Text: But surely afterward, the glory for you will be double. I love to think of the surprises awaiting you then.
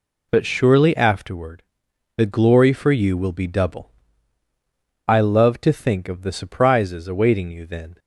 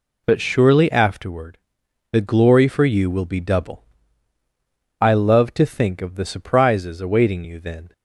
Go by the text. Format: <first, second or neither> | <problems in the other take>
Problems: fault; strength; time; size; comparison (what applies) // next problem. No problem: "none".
neither | none